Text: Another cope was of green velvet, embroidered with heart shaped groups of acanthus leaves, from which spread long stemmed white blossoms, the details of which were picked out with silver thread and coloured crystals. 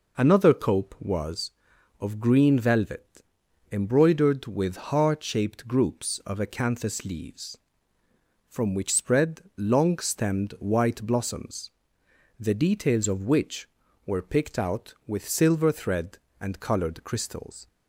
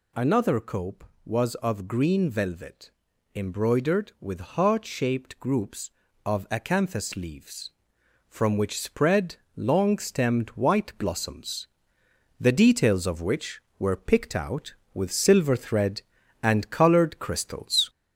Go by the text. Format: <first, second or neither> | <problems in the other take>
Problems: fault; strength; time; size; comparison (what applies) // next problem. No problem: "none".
first | gets louder; noticeable; throughout; 4 dB // pauses between "spread" and "long"; slight; at 9.3 s; 0.18 s long; slight in the first